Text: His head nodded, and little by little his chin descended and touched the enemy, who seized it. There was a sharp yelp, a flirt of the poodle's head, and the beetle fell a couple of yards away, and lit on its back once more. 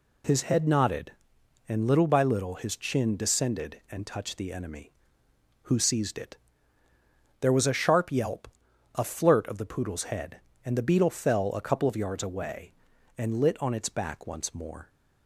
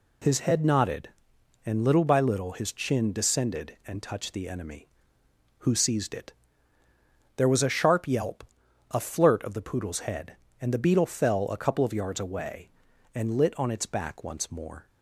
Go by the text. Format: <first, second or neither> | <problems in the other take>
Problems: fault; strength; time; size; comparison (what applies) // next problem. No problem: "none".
neither | none